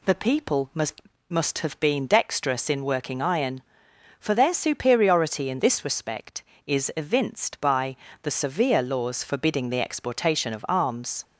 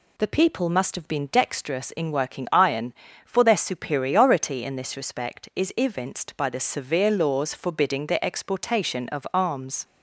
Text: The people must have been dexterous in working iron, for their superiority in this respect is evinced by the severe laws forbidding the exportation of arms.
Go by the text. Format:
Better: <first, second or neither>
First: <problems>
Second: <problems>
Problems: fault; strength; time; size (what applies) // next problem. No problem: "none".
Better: second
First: says "must" twice; at 1.2 s // pauses between "by" and "the"; slight; at 7.9 s; 0.28 s long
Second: none